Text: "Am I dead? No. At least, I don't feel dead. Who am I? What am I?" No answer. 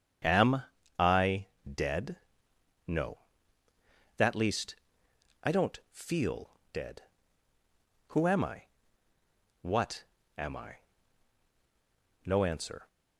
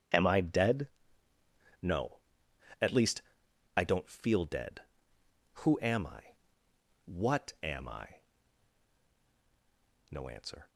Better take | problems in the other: second | starts louder than the rest; strong; until 1.7 s; 7.5 dB // pauses between "Am" and "I"; slight; at 0.6 s; 0.34 s long // pauses between "I" and "dead"; slight; at 1.4 s; 0.22 s long // says "That" for "At"; at 4.1 s // pauses between "feel" and "dead"; slight; at 6.5 s; 0.20 s long // pauses between "What" and "am"; slight; at 10.0 s; 0.32 s long

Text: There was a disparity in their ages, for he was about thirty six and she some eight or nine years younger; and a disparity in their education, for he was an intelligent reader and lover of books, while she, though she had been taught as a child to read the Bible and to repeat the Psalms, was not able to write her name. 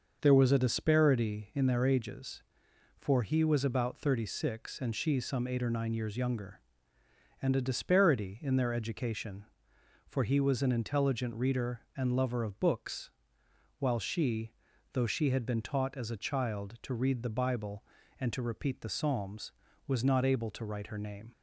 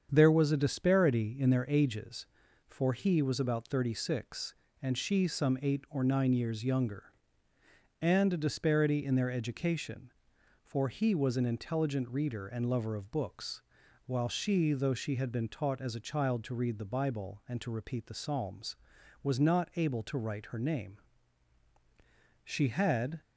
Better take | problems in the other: first | starts louder than the rest; strong; until 1.1 s; 7.5 dB; noticeable in the first // goes on to say "She had"; noticeable; from 22.4 s on; 0.76 s long

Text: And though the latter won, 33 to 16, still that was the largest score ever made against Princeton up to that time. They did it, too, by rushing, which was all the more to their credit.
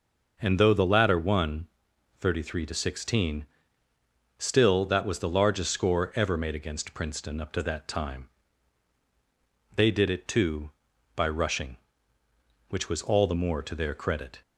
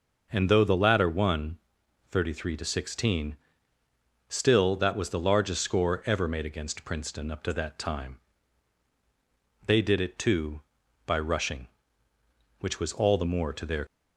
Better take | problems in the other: first | stops before "credit"; at 13.8 s

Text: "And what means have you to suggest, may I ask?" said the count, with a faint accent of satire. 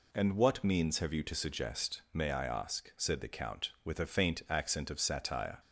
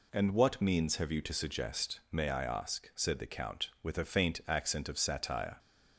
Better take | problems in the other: neither | none

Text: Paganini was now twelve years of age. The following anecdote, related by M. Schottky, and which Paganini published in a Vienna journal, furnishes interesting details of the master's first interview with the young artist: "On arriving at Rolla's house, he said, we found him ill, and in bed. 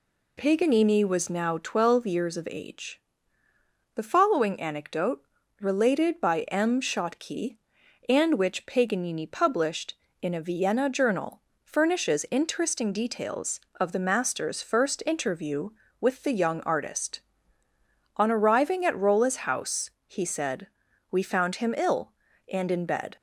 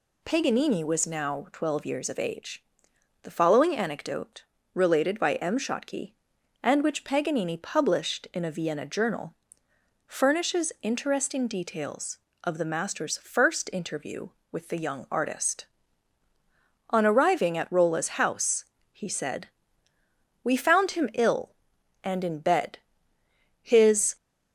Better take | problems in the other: first | goes on to say "His"; from 23.6 s on; 0.54 s long

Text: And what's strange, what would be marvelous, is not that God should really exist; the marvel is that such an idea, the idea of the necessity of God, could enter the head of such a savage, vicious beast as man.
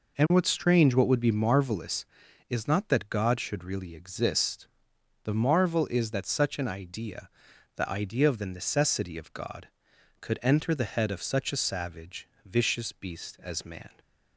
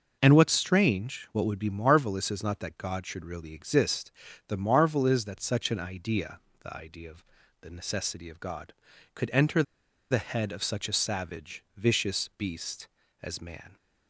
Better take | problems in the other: first | pauses between "of" and "the"; at 7.2 s; 0.38 s long // pauses between "enter" and "the"; noticeable; at 9.6 s; 0.48 s long

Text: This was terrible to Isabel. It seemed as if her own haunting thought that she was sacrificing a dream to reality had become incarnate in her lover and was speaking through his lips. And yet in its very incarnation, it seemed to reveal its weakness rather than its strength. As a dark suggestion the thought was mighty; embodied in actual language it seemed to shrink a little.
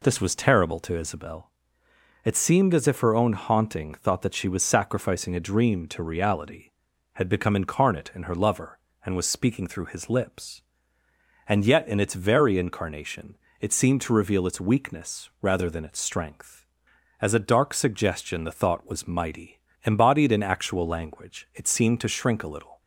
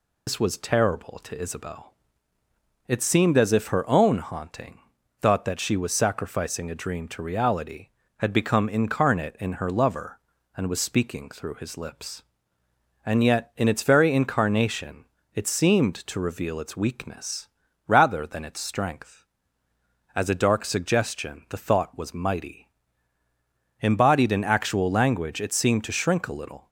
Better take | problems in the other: first | loses the start of "This"; at 0.2 s; 75 ms // pauses between "haunting" and "thought"; at 4.7 s; 0.42 s long // pauses between "weakness" and "rather"; at 17.4 s; 0.40 s long

